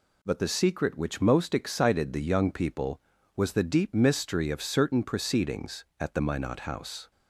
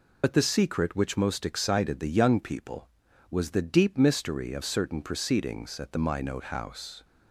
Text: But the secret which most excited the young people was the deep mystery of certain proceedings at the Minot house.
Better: first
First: none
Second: loses the start of "But"; at 0.2 s; 40 ms

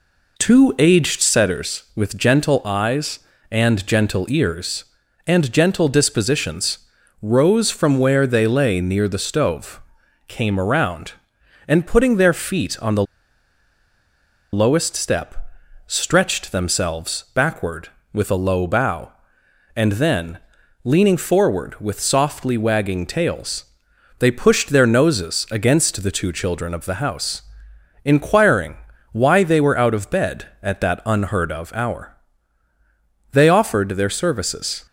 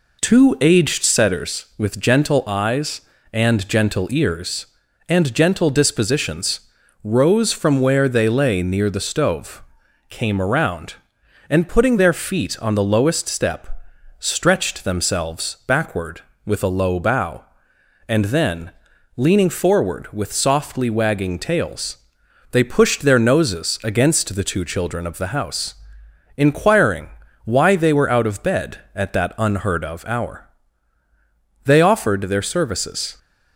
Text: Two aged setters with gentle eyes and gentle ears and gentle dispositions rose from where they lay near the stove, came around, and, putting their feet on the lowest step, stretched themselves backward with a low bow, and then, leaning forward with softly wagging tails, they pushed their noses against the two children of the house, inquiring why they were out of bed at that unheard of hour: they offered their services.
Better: second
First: pauses between "dispositions" and "rose"; at 6.7 s; 0.44 s long // pauses between "the" and "lowest"; strong; at 13.0 s; 1.4 s long // pauses between "inquiring" and "why"; slight; at 28.7 s; 0.34 s long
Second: pauses between "dispositions" and "rose"; at 6.5 s; 0.44 s long // pauses between "inquiring" and "why"; slight; at 27.0 s; 0.34 s long

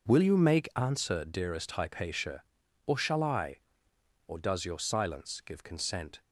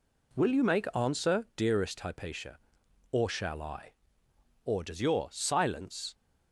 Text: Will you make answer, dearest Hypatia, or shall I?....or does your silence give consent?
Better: first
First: none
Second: stops before "give consent"; at 6.1 s

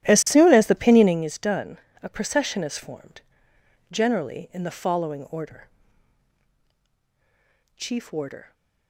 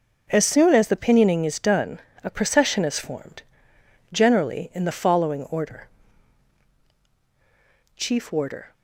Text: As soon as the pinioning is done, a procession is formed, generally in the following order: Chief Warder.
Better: second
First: starts louder than the rest; strong; until 1.3 s; 13 dB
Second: none

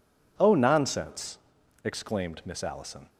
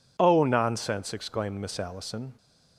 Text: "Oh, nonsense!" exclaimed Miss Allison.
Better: neither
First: none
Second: none

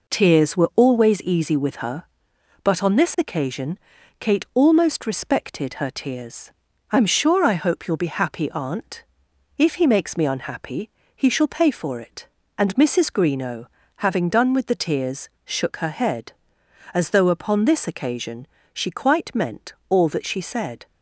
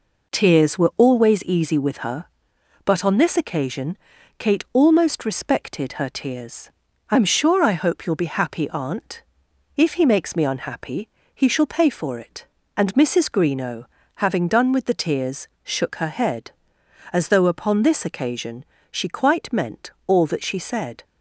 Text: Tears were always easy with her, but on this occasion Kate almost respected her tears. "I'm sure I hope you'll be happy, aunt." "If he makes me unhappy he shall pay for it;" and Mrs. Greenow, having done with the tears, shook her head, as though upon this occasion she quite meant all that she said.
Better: neither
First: pauses between "occasion" and "Kate"; at 3.7 s; 0.42 s long // pauses between "unhappy" and "he"; slight; at 10.8 s; 0.26 s long // pauses between "occasion" and "she"; slight; at 18.4 s; 0.26 s long // pauses between "meant" and "all"; slight; at 19.7 s; 0.16 s long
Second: pauses between "occasion" and "Kate"; at 3.9 s; 0.42 s long // pauses between "unhappy" and "he"; slight; at 11.0 s; 0.26 s long // pauses between "occasion" and "she"; slight; at 18.6 s; 0.26 s long // pauses between "meant" and "all"; slight; at 19.9 s; 0.16 s long

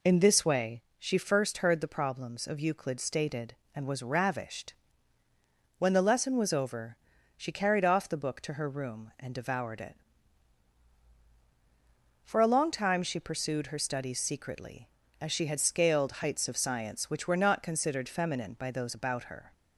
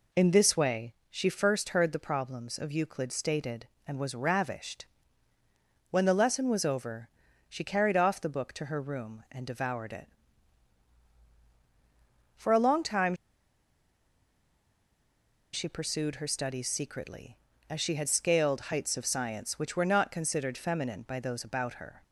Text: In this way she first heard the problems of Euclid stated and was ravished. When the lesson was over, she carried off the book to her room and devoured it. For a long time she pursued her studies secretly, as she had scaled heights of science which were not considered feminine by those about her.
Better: first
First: pauses between "way" and "she"; slight; at 0.8 s; 0.16 s long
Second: pauses between "way" and "she"; slight; at 0.9 s; 0.16 s long // pauses between "time" and "she"; strong; at 13.1 s; 2.3 s long

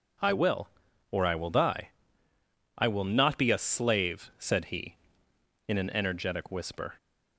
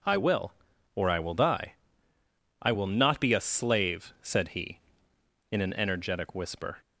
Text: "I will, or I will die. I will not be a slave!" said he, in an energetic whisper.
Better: neither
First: none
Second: none

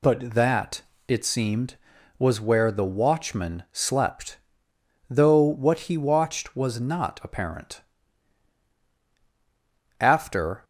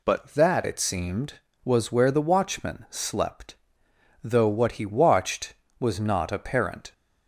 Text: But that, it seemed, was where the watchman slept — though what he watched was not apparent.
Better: second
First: goes on to say "After"; noticeable; from 9.9 s on; 0.64 s long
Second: none

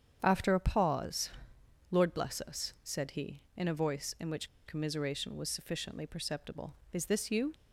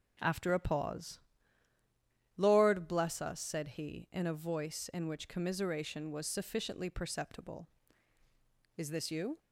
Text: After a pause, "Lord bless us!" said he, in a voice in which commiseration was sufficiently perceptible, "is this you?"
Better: second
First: starts louder than the rest; strong; until 1.2 s; 8 dB // pauses between "which" and "commiseration"; slight; at 4.4 s; 0.19 s long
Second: none

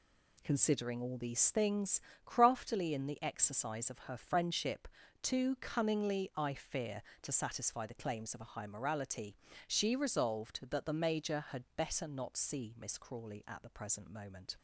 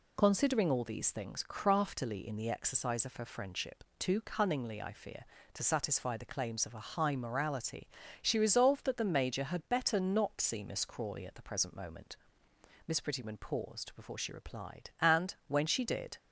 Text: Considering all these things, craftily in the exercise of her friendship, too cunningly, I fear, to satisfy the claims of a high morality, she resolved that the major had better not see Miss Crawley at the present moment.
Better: first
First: none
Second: goes on to say "Miss Prettyman paused before she replied and when she did"; strong; from 12.8 s on; 3.3 s long

